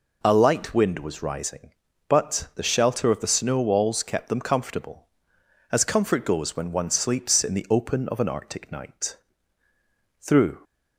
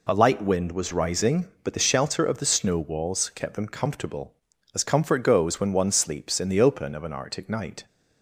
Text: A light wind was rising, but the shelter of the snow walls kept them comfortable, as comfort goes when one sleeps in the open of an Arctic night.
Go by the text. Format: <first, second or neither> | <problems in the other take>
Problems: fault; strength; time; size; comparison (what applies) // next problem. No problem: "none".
second | goes on to say "Through"; slight; from 10.1 s on; 0.40 s long